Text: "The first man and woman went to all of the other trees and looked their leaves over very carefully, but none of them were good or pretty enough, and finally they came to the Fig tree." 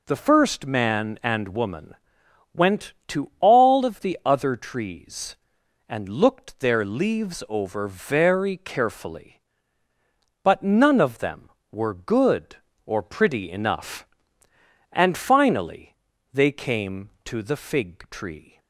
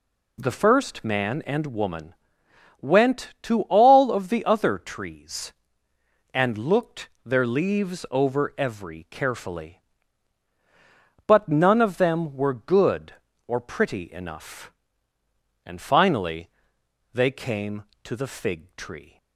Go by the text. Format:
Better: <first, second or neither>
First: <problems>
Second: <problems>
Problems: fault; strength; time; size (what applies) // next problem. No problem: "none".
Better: first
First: pauses between "woman" and "went"; noticeable; at 1.9 s; 0.58 s long // pauses between "finally" and "they"; at 15.9 s; 0.38 s long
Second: pauses between "woman" and "went"; noticeable; at 2.1 s; 0.64 s long // pauses between "looked" and "their"; slight; at 7.0 s; 0.16 s long // says "every" for "very"; at 8.5 s // pauses between "finally" and "they"; noticeable; at 16.4 s; 0.64 s long